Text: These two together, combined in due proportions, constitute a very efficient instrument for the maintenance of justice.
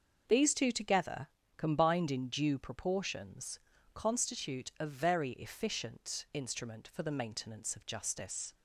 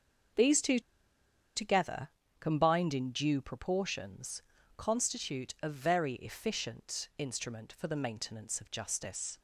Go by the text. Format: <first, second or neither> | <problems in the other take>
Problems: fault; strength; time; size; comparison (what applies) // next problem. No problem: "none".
first | starts louder than the rest; until 2.4 s; 6.5 dB; also in the first // pauses between "two" and "together"; noticeable; at 0.7 s; 0.76 s long